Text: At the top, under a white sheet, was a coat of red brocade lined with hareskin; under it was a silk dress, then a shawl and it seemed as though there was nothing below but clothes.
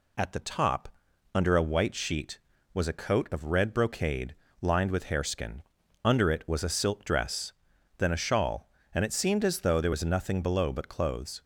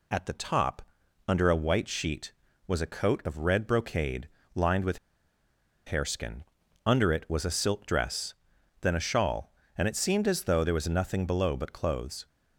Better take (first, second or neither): first